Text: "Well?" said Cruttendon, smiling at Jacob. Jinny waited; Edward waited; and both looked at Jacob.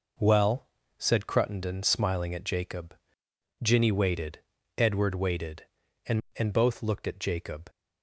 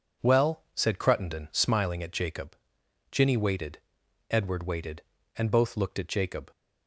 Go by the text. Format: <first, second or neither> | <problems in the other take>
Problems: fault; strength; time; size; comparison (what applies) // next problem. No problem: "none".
second | says "and" twice; at 6.3 s